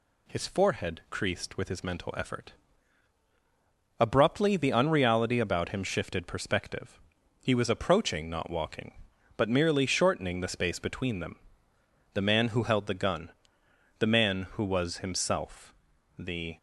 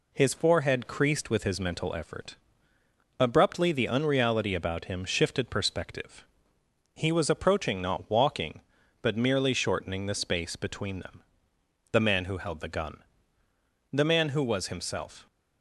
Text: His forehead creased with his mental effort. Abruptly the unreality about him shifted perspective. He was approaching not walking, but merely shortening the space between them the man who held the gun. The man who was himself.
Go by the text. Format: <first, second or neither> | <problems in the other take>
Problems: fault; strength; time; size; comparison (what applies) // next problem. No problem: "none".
second | pauses between "them" and "the"; noticeable; at 11.3 s; 0.74 s long; noticeable in the second // goes on to say "The"; slight; from 16.1 s on; 0.40 s long